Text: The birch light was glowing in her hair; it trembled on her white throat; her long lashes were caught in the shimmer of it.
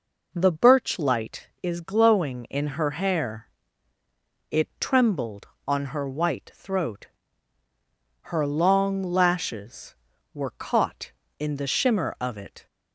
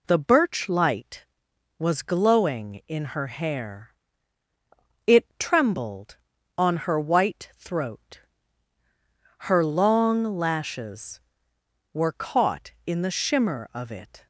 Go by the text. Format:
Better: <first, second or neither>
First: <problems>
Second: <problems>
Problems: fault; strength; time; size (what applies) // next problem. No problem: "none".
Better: second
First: says "is" for "was"; at 1.6 s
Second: none